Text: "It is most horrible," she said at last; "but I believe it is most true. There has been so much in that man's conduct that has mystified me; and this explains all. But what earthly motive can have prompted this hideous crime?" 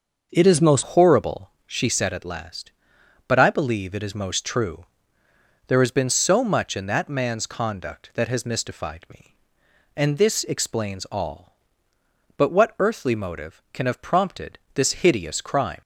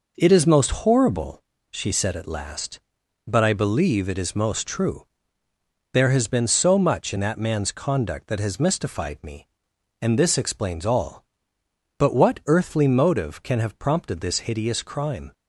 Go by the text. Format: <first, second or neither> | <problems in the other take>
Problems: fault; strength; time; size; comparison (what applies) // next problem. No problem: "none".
second | starts louder than the rest; until 1.3 s; 6 dB // changes voice at "horrible"; from 0.8 s on; 15.0 s long // pauses between "prompted" and "this"; slight; at 14.5 s; 0.16 s long